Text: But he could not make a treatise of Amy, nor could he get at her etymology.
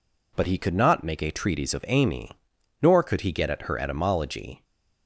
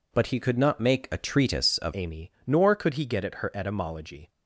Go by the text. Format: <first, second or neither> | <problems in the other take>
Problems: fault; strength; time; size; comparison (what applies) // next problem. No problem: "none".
first | changes voice at "Amy"; from 1.9 s on; 2.3 s long